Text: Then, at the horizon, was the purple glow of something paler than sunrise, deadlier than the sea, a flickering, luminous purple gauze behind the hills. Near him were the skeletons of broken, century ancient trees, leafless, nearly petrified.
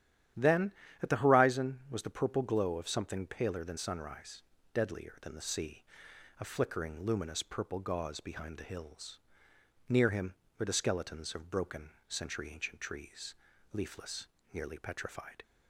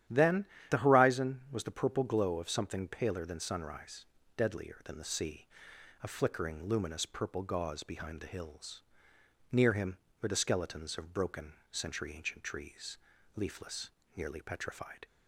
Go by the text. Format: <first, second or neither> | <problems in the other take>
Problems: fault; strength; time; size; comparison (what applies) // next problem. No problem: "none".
first | starts louder than the rest; strong; until 1.3 s; 11 dB; strong in the first // skips "at"; at 0.5 s